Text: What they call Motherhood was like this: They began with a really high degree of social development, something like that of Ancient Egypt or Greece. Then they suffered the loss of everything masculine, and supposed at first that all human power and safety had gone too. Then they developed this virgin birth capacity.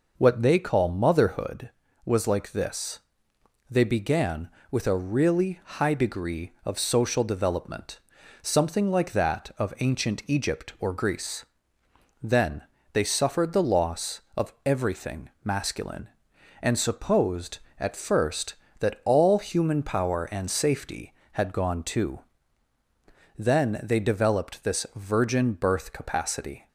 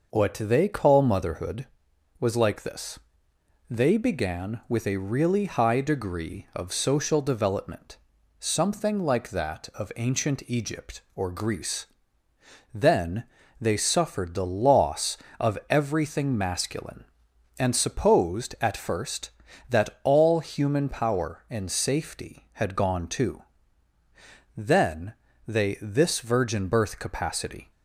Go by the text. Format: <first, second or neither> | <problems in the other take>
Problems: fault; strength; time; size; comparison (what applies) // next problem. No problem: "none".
first | pauses between "Then" and "they"; at 13.2 s; 0.38 s long; slight in the first // pauses between "Then" and "they"; slight; at 25.1 s; 0.34 s long // skips "developed"; at 25.7 s